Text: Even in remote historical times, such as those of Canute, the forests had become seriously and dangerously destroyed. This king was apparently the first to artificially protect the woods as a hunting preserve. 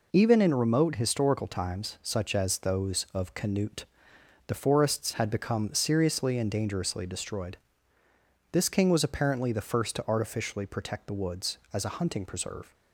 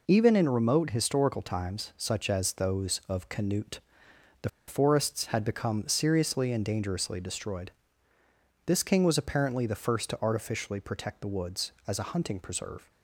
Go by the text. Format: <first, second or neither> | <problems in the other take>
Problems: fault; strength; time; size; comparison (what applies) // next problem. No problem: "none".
first | pauses between "the" and "forests"; slight; at 4.4 s; 0.18 s long